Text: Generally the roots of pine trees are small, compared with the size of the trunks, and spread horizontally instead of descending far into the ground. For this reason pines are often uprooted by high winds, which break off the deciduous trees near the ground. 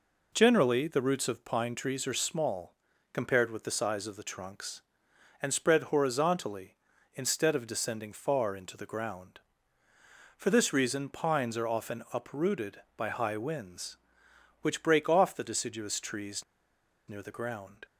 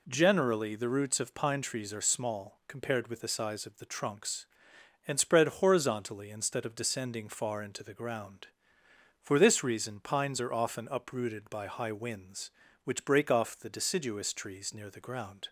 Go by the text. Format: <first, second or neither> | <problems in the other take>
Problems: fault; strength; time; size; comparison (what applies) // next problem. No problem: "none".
second | pauses between "trees" and "near"; noticeable; at 16.4 s; 0.64 s long